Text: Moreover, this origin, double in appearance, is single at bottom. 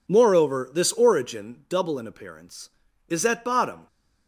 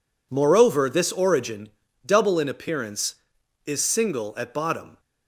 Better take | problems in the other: second | skips "single"; at 3.2 s

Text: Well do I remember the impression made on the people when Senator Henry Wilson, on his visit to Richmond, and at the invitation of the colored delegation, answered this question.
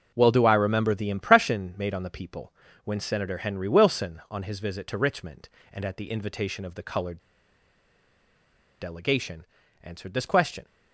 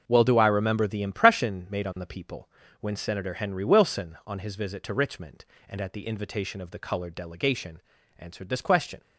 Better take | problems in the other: second | pauses between "people" and "when"; slight; at 2.5 s; 0.32 s long; slight in the second // pauses between "colored" and "delegation"; strong; at 7.1 s; 1.6 s long

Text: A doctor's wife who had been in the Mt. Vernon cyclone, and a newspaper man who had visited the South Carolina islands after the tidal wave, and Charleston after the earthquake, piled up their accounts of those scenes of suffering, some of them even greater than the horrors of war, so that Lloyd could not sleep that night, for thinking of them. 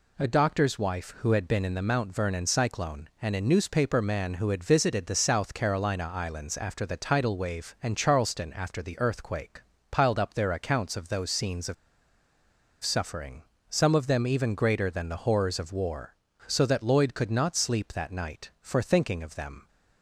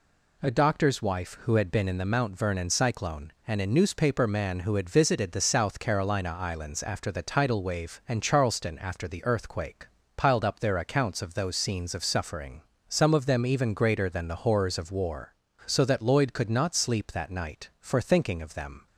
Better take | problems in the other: second | pauses between "of" and "suffering"; at 11.7 s; 1.0 s long

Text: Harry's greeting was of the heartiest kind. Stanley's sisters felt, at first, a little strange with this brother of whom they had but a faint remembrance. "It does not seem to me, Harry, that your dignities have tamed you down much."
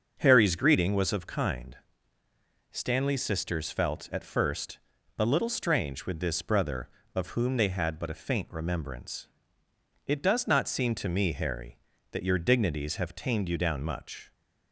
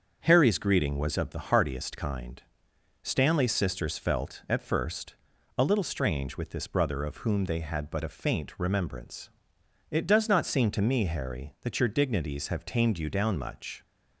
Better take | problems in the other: second | starts louder than the rest; until 1.2 s; 6.5 dB; also in the second // skips "the heartiest"; at 1.2 s

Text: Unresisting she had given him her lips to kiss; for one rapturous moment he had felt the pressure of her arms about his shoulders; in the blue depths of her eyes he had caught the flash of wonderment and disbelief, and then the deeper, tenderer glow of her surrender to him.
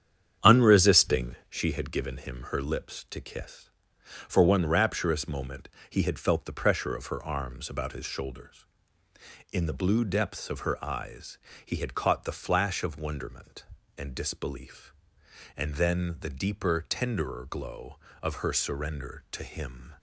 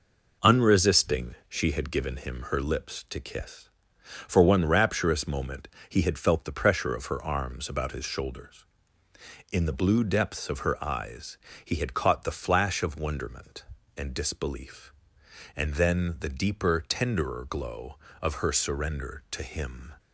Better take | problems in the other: second | starts louder than the rest; strong; until 1.6 s; 9 dB // pauses between "moment" and "he"; slight; at 5.6 s; 0.22 s long; slight in the second // pauses between "eyes" and "he"; slight; at 11.3 s; 0.28 s long; slight in the second

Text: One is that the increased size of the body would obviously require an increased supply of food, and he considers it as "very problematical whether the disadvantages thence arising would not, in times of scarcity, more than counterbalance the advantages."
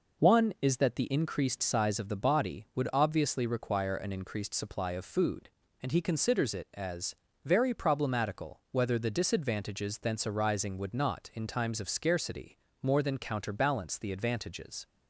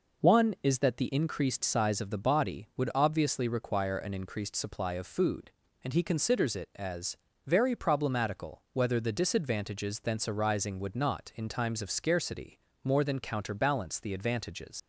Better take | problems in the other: first | pauses between "as" and "very"; slight; at 7.1 s; 0.30 s long; slight in the first // leaves "advantages" unfinished; at 14.7 s; 75 ms

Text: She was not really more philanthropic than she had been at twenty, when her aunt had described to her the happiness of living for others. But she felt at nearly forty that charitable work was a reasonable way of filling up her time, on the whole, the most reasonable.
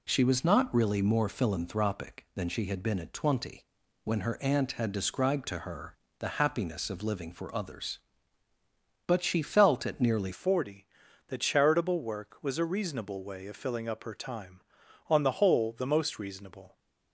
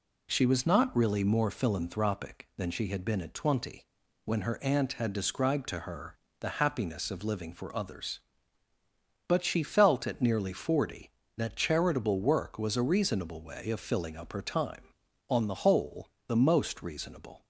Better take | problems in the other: second | pauses between "her" and "the"; slight; at 5.9 s; 0.22 s long; slight in the second // changes voice at "forty"; from 10.3 s on; 6.4 s long

